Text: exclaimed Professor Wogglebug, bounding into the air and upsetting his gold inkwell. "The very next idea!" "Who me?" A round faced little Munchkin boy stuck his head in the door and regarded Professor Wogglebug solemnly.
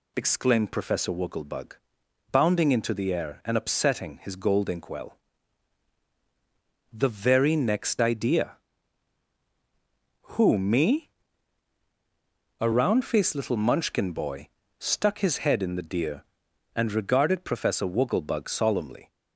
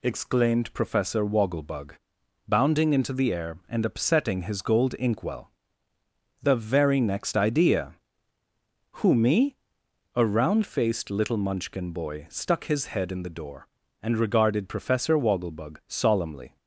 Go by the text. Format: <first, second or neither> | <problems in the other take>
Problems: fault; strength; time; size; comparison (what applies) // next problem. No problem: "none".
second | pauses between "boy" and "stuck"; slight; at 14.4 s; 0.32 s long // says "deer" for "door"; at 15.8 s